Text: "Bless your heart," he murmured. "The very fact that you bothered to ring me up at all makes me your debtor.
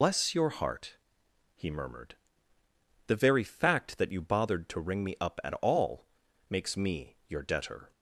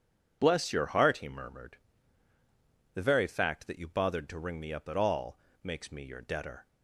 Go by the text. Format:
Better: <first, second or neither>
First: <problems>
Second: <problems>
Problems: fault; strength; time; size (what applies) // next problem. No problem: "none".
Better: second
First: loses the start of "Bless"; at 0.0 s; 100 ms // pauses between "all" and "makes"; at 6.0 s; 0.42 s long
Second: pauses between "all" and "makes"; slight; at 5.3 s; 0.24 s long